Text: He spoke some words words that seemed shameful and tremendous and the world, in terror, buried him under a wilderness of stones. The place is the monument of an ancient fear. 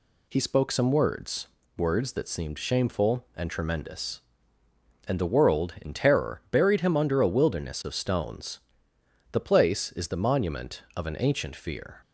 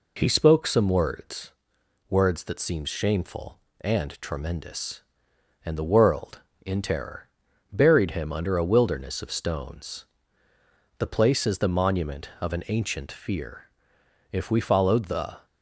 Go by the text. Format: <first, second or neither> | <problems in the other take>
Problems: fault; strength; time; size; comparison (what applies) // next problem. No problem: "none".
first | pauses between "words" and "words"; noticeable; at 1.5 s; 0.58 s long; slight in the first // goes on to say "If we followed the"; noticeable; from 14.2 s on; 1.1 s long